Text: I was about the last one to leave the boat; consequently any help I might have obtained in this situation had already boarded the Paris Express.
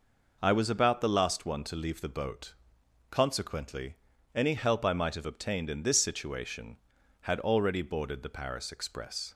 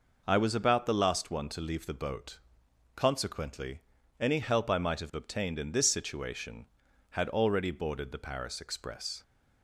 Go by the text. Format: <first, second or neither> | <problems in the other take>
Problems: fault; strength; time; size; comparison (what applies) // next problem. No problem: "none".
neither | pauses between "consequently" and "any"; the same in both